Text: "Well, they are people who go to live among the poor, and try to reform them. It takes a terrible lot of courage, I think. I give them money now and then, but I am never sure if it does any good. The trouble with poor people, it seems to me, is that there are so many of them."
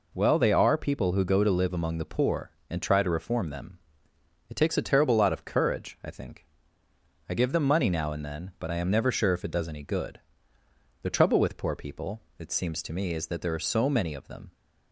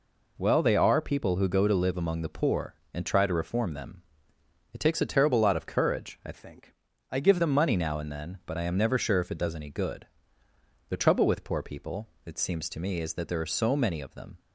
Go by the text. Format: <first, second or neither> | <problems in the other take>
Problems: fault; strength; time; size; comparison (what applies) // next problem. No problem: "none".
first | changes voice from "think" to "give"; from 6.3 to 7.3 s; 1.0 s long